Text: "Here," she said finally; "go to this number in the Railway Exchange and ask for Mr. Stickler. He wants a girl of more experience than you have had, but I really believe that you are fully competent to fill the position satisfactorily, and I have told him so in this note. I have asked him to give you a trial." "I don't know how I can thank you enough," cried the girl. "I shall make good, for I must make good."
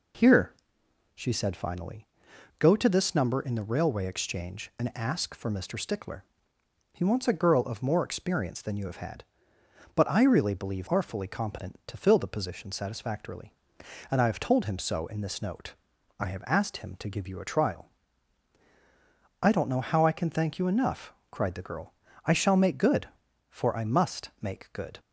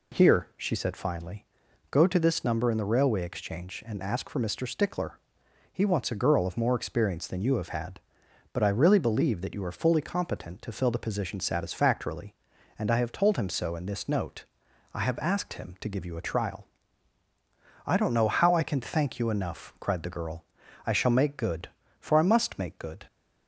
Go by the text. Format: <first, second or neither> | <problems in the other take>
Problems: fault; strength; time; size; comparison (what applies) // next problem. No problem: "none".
second | skips "that you"; at 10.8 s